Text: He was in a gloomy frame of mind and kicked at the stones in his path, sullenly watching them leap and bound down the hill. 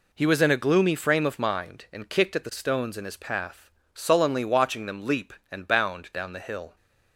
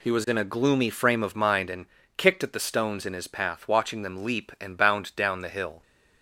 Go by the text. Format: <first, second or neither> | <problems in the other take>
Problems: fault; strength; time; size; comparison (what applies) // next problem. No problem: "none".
first | pauses between "and" and "kicked"; slight; at 1.8 s; 0.32 s long // skips "sullenly"; at 3.6 s